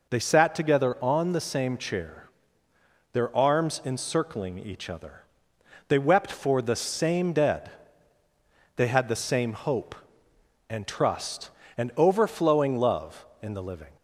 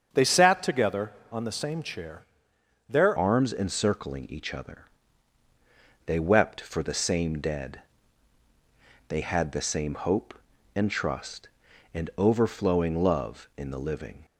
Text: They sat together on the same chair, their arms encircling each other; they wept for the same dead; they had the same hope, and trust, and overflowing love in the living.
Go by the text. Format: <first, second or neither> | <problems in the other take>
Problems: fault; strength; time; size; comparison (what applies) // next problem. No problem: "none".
first | starts louder than the rest; strong; until 1.1 s; 7.5 dB // changes voice at "arms"; from 3.1 s on; 11.1 s long